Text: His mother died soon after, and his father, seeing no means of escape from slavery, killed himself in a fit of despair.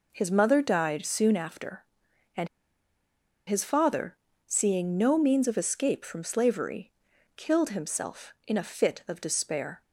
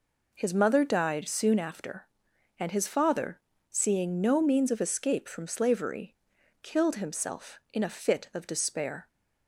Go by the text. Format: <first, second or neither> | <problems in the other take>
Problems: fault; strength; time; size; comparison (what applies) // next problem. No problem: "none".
second | pauses between "and" and "his"; at 2.4 s; 0.99 s long